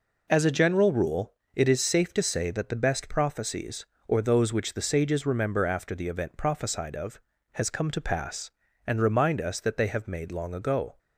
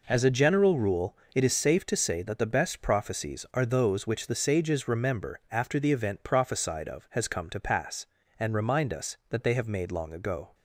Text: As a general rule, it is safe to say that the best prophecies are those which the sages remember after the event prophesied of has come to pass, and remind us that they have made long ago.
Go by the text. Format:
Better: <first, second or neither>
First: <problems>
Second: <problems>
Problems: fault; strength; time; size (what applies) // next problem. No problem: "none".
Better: second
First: says "or" for "are"; at 4.0 s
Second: none